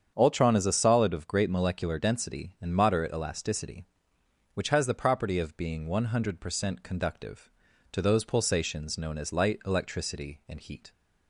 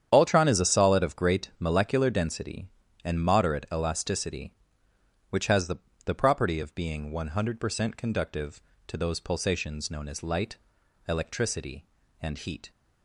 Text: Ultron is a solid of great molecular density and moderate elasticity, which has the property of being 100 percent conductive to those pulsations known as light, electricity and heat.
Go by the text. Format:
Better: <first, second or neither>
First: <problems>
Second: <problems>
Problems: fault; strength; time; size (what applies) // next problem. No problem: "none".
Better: first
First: starts louder than the rest; strong; until 1.1 s; 7.5 dB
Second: starts louder than the rest; strong; until 1.1 s; 9 dB // says "the" twice; at 6.0 s